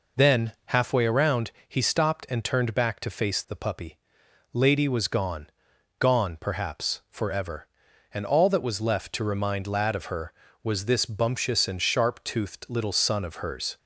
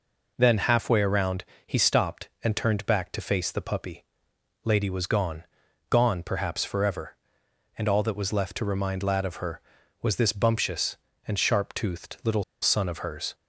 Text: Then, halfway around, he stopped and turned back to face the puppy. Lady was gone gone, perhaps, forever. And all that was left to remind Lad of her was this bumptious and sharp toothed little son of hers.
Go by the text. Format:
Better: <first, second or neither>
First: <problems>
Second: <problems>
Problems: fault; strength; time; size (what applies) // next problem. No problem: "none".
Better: first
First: pauses between "gone" and "gone"; noticeable; at 5.4 s; 0.52 s long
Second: pauses between "gone" and "gone"; noticeable; at 5.4 s; 0.46 s long // pauses between "little" and "son"; slight; at 12.4 s; 0.19 s long